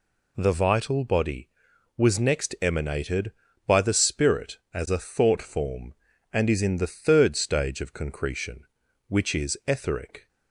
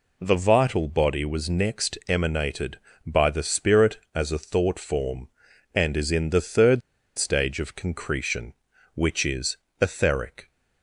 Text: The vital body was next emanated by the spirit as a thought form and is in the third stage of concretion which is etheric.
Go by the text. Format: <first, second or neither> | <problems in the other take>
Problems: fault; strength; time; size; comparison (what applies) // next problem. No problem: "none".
first | pauses between "third" and "stage"; at 6.8 s; 0.36 s long // pauses between "is" and "etheric"; slight; at 9.5 s; 0.24 s long